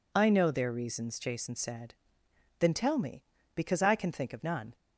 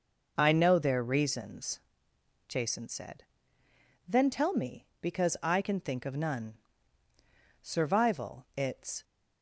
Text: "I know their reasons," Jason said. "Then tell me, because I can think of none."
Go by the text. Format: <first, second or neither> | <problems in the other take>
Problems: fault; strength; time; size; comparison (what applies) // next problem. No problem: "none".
first | goes on to say "Survival it's"; from 7.6 s on; 1.4 s long